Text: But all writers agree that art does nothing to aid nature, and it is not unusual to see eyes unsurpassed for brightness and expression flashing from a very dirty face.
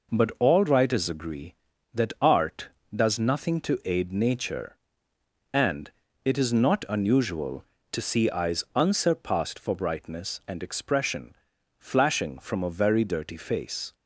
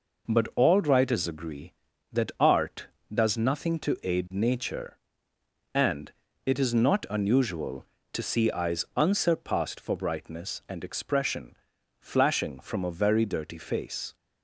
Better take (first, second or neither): neither